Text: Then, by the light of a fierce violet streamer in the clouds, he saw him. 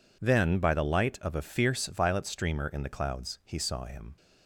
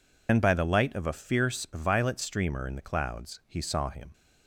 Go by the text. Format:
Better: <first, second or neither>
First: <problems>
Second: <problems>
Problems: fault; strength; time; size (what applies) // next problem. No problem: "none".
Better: first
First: none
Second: loses the start of "Then"; at 0.2 s; 85 ms